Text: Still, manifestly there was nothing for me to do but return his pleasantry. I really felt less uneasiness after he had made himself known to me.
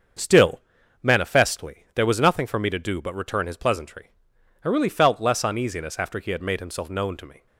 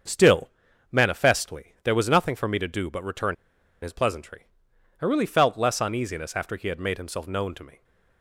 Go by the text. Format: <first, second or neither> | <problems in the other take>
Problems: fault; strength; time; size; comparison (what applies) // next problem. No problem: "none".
first | starts louder than the rest; until 1.5 s; 7 dB; also in the first // pauses between "return" and "his"; noticeable; at 3.3 s; 0.47 s long